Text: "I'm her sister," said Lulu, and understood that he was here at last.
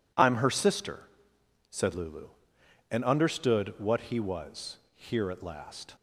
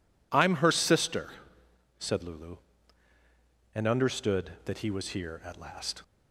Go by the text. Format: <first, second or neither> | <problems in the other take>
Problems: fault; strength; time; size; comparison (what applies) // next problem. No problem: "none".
second | says "what" for "that"; at 3.7 s // pauses between "was" and "here"; slight; at 4.7 s; 0.16 s long